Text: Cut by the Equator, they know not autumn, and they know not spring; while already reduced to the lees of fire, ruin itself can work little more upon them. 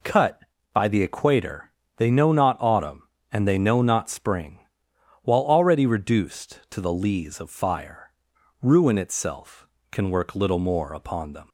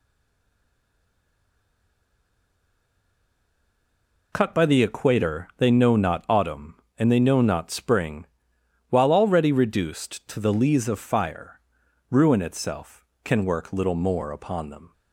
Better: first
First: none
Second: stays silent before the first word; strong; until 4.3 s; 4.3 s long

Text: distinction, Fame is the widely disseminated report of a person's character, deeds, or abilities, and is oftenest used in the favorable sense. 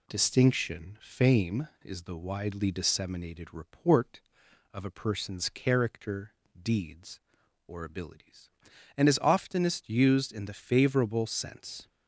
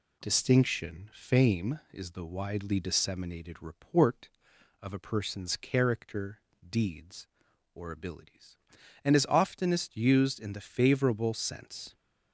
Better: neither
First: none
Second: none

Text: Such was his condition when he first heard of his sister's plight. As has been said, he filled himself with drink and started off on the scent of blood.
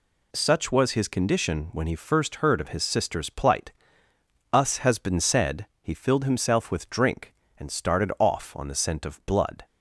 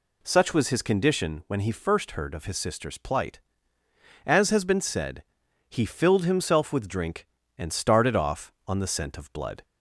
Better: second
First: says "Us" for "As"; at 4.5 s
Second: none

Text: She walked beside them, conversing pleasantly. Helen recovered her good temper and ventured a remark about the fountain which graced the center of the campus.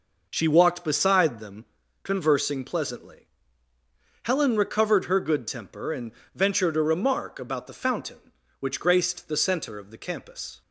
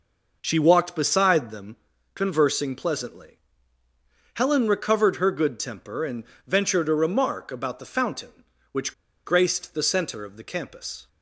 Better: first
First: pauses between "and" and "ventured"; slight; at 6.1 s; 0.22 s long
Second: pauses between "and" and "ventured"; slight; at 6.2 s; 0.22 s long // pauses between "which" and "graced"; slight; at 8.9 s; 0.32 s long

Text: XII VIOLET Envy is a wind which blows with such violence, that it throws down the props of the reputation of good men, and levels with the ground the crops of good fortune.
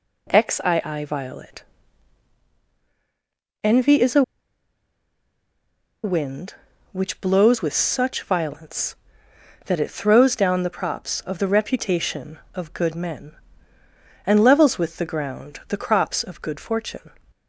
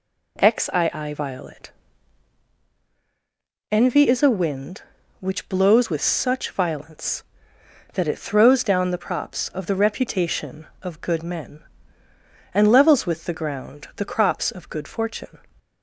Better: second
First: pauses between "VIOLET" and "Envy"; strong; at 1.6 s; 2.0 s long // pauses between "a" and "wind"; strong; at 4.2 s; 1.8 s long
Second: pauses between "VIOLET" and "Envy"; strong; at 1.6 s; 2.0 s long

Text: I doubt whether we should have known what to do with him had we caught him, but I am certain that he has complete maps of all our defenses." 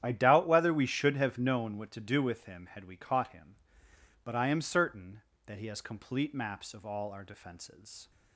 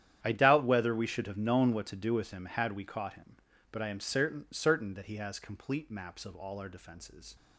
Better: first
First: starts louder than the rest; strong; until 1.0 s; 10 dB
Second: starts louder than the rest; strong; until 1.2 s; 10.5 dB // says "certain" twice; at 4.5 s

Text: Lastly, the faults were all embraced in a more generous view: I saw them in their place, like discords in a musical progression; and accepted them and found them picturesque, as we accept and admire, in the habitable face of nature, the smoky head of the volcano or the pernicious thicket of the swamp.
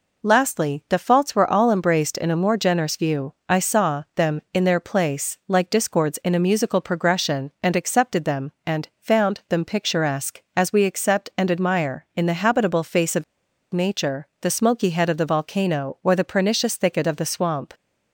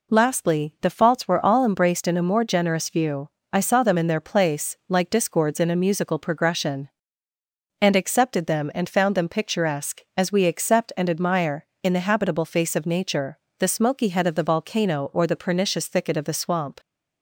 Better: second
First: pauses between "of" and "nature"; noticeable; at 13.2 s; 0.50 s long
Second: none

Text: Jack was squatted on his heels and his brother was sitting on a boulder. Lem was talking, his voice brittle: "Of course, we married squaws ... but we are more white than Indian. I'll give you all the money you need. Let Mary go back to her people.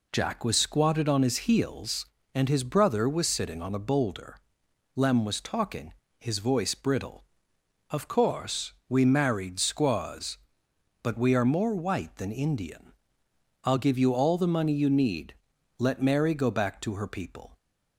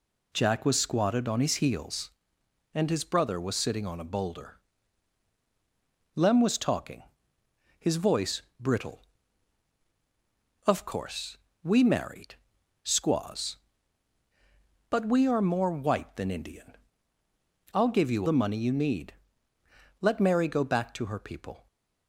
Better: first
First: none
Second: pauses between "voice" and "brittle"; slight; at 8.3 s; 0.18 s long // pauses between "married" and "squaws"; noticeable; at 12.3 s; 0.46 s long // skips "all"; at 18.2 s

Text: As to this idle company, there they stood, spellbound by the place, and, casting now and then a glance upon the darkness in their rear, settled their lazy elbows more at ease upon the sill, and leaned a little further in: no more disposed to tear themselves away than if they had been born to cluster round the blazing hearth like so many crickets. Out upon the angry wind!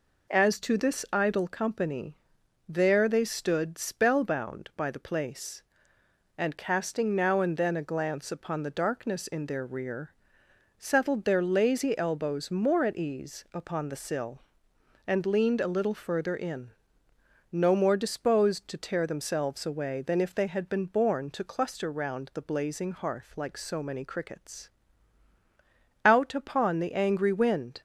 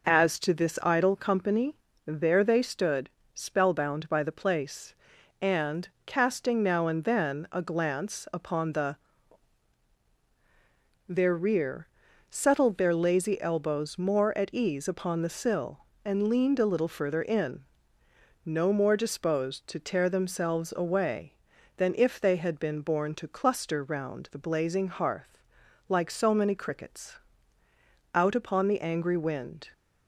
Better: first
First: none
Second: skips "darkness in"; at 10.0 s // pauses between "hearth" and "like"; noticeable; at 25.4 s; 0.48 s long

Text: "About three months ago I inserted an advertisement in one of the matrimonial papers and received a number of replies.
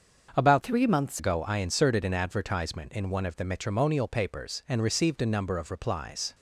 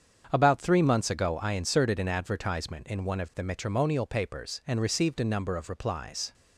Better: second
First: starts louder than the rest; until 1.3 s; 7 dB // changes voice from "three" to "months"; from 0.6 to 1.1 s; 0.5 s long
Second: starts louder than the rest; strong; until 1.3 s; 7.5 dB

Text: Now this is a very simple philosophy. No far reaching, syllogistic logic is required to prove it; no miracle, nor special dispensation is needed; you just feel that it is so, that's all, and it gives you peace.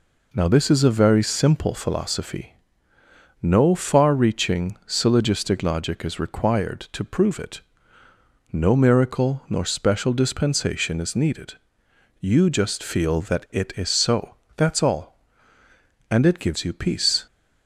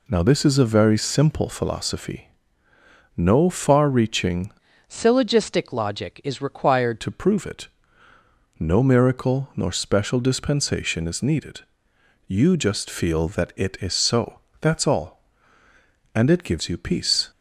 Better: first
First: none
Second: changes voice from "syllogistic" to "required"; from 4.8 to 7.0 s; 2.2 s long

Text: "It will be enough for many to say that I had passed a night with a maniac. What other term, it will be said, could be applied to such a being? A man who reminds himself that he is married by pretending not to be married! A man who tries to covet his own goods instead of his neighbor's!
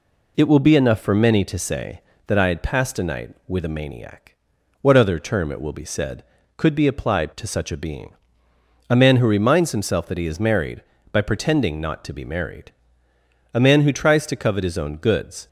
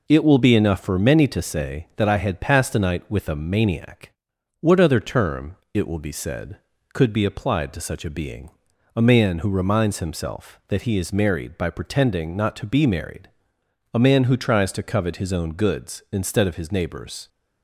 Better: second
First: stops before "instead of his neighbor's"; at 15.4 s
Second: none

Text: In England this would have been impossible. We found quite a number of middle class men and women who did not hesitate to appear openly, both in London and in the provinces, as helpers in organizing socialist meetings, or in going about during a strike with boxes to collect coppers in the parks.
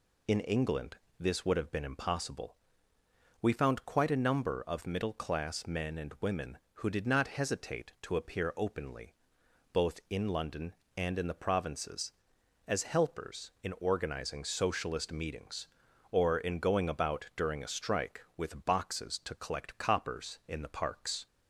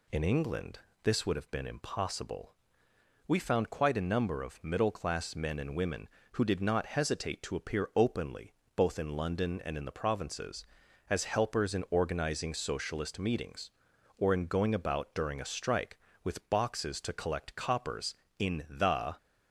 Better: first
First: pauses between "England" and "this"; slight; at 0.9 s; 0.22 s long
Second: pauses between "England" and "this"; slight; at 0.7 s; 0.24 s long // stops before "parks"; at 19.1 s

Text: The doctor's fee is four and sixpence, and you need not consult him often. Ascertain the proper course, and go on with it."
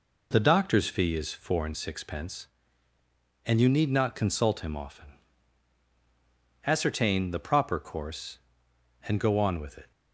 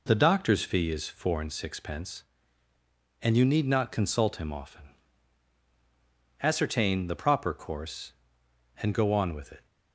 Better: neither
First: none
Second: none

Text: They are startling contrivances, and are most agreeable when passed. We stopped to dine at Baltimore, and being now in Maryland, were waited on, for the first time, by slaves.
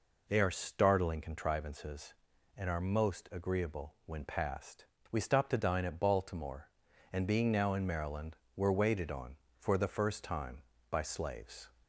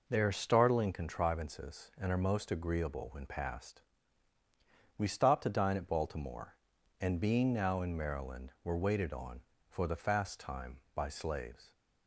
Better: first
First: none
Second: says "fast" for "first"; at 9.9 s

